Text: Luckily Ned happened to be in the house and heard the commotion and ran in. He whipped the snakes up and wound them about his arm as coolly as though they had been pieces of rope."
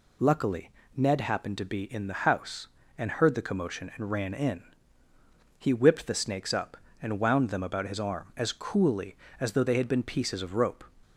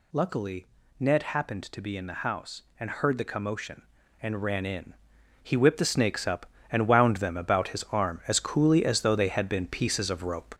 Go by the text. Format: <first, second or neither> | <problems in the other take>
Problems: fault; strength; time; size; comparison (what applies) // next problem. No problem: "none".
first | gets louder; noticeable; throughout; 4.5 dB // pauses between "Luckily" and "Ned"; slight; at 0.6 s; 0.34 s long; slight in the first